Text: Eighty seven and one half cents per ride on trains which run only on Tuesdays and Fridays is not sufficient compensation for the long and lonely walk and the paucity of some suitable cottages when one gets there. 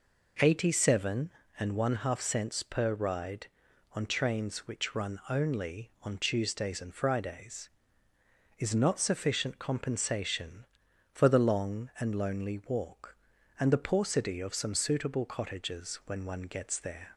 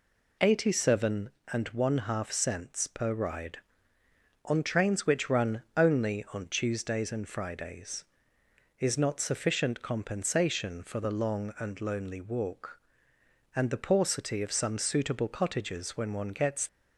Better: first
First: none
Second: stops before "there"; at 16.6 s

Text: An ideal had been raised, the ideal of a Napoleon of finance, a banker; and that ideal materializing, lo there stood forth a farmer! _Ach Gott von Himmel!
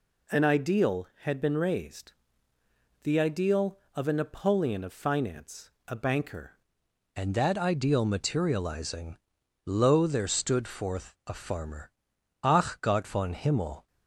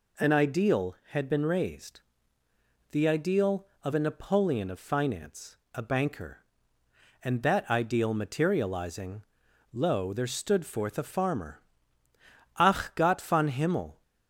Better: second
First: changes voice at "and"; from 7.1 s on; 6.7 s long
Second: none

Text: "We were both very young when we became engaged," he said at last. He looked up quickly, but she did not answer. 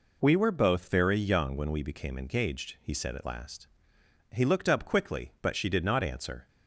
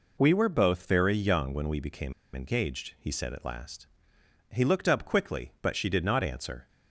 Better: first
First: none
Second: pauses between "became" and "engaged"; slight; at 2.1 s; 0.22 s long

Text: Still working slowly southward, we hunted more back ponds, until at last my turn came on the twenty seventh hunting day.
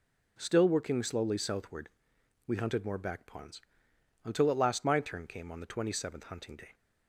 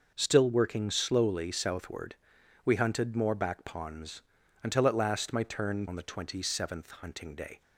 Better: first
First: none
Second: skips "came"; at 5.8 s

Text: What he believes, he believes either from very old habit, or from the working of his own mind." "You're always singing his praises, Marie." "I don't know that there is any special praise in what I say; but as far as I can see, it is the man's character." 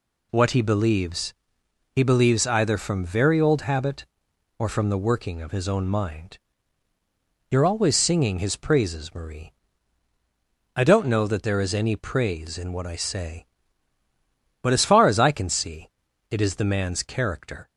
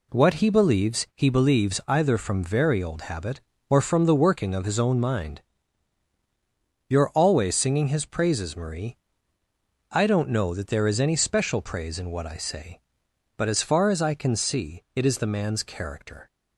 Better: second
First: skips "special"; at 11.9 s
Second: none

